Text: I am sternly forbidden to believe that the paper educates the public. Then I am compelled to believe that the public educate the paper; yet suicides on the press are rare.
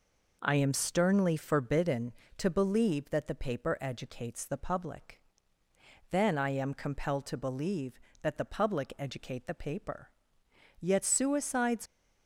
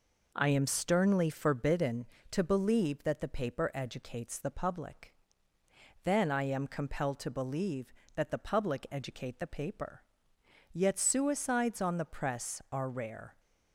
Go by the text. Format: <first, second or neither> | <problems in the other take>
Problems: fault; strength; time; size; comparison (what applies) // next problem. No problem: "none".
second | stops before "on the press are rare"; at 11.8 s